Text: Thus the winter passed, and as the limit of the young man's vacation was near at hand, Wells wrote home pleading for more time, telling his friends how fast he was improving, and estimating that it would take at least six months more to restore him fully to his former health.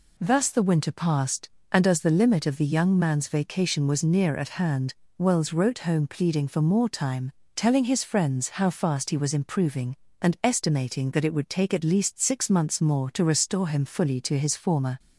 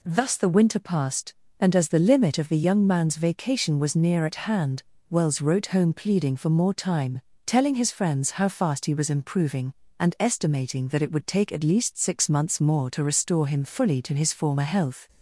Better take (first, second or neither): second